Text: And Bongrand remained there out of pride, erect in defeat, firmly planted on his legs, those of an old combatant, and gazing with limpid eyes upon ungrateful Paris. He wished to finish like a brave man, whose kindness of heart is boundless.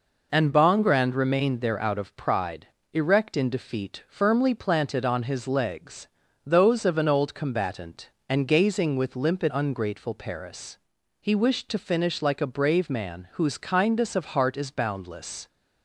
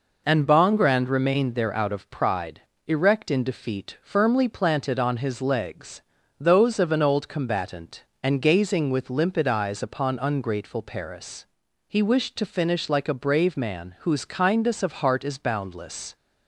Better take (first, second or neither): second